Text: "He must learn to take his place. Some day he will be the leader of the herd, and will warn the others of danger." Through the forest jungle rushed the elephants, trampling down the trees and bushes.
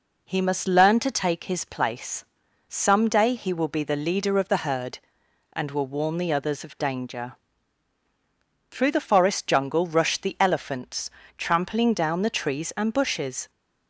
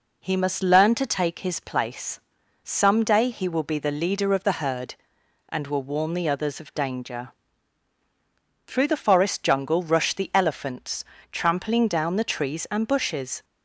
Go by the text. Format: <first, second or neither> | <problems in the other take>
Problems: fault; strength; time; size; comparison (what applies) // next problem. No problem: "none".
neither | none